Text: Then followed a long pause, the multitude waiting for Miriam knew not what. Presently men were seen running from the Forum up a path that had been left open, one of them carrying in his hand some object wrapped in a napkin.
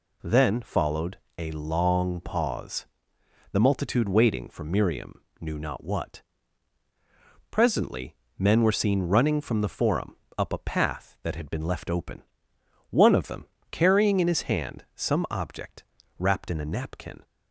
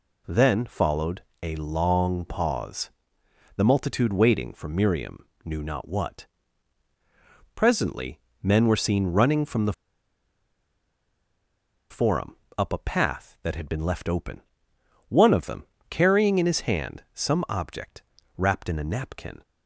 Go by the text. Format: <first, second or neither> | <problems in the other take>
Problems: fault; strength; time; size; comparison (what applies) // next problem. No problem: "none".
first | pauses between "followed" and "a"; slight; at 1.2 s; 0.20 s long; slight in the first // pauses between "Miriam" and "knew"; slight; at 5.2 s; 0.18 s long; slight in the first // pauses between "Presently" and "men"; slight; at 8.1 s; 0.24 s long; slight in the first // pauses between "the" and "Forum"; strong; at 9.7 s; 2.1 s long // pauses between "Forum" and "up"; slight; at 12.3 s; 0.22 s long; slight in the first // pauses between "them" and "carrying"; slight; at 15.6 s; 0.26 s long; slight in the first // pauses between "object" and "wrapped"; slight; at 18.0 s; 0.36 s long; slight in the first